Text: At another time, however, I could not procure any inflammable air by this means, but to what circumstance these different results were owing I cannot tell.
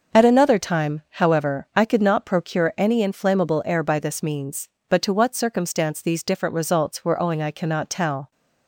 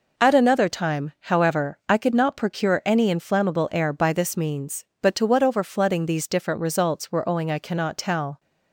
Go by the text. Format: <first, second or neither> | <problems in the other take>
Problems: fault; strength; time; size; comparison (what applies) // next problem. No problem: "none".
first | says "overflooding" for "circumstance"; at 5.4 s